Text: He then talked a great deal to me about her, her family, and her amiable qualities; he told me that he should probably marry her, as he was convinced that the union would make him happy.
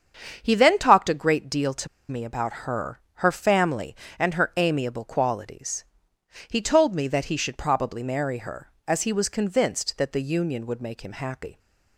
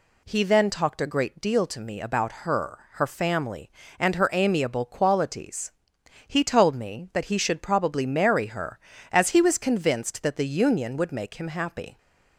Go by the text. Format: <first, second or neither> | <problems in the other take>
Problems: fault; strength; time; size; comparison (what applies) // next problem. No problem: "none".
second | starts louder than the rest; strong; until 1.4 s; 7.5 dB // pauses between "to" and "me"; slight; at 1.8 s; 0.22 s long